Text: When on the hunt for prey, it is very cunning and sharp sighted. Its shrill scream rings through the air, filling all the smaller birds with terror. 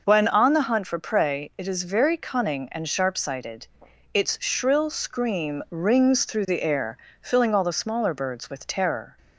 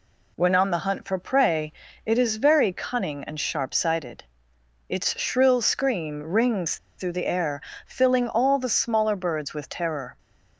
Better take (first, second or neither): first